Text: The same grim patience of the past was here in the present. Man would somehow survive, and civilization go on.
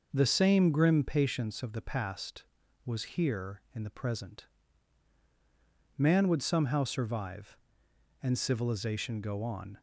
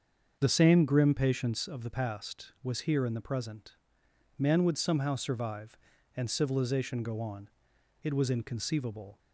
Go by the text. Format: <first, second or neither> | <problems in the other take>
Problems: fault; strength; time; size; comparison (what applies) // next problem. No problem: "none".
first | starts louder than the rest; until 1.4 s; 6.5 dB // goes on to say "It was inconceivable"; noticeable; from 8.0 s on; 1.1 s long